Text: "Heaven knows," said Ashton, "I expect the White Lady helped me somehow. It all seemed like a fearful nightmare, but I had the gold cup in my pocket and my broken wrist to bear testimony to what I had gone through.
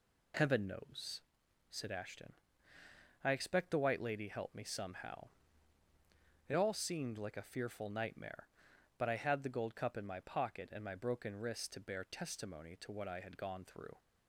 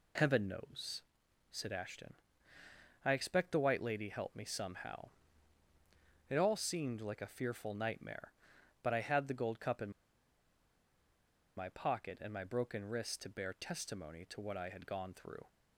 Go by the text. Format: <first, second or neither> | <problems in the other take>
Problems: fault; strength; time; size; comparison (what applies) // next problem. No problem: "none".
first | pauses between "in" and "my"; strong; at 9.9 s; 1.6 s long